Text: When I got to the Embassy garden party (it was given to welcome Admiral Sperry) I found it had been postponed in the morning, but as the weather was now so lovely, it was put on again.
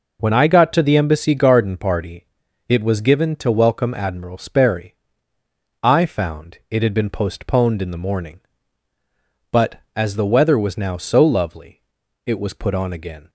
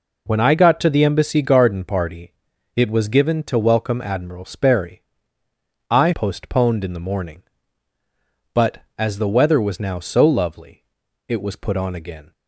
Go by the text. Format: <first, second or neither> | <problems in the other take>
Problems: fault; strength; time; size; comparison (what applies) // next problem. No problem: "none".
first | skips "found it had been"; at 6.1 s